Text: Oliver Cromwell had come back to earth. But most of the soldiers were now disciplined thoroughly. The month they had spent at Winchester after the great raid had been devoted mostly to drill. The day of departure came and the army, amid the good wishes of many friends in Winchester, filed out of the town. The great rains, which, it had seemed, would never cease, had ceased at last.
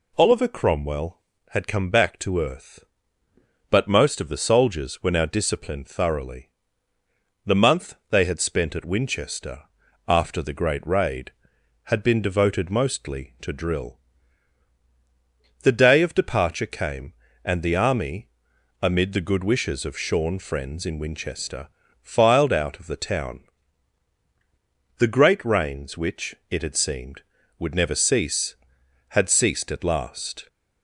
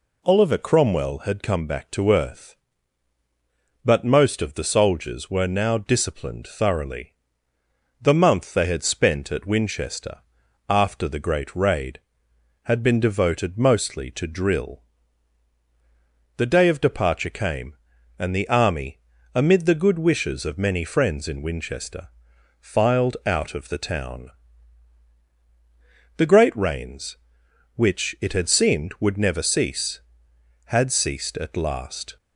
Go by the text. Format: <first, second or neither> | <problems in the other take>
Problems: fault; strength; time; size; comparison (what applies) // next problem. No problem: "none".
second | pauses between "month" and "they"; slight; at 7.9 s; 0.16 s long // pauses between "Winchester" and "after"; at 9.6 s; 0.44 s long; noticeable in the second // says "shorn" for "many"; at 19.9 s